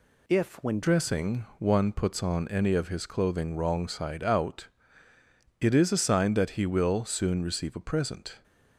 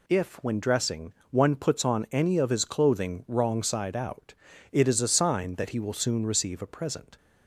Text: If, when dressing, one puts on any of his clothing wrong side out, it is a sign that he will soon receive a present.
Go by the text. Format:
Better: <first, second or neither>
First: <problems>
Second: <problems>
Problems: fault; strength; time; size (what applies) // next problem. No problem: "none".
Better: second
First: changes voice at "dressing"; from 0.8 s on; 7.6 s long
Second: none